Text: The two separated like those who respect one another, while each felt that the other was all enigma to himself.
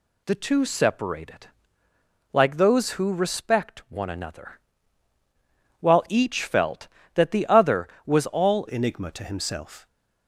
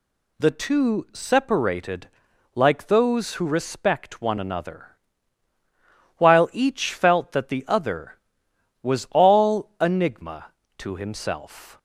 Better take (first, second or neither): second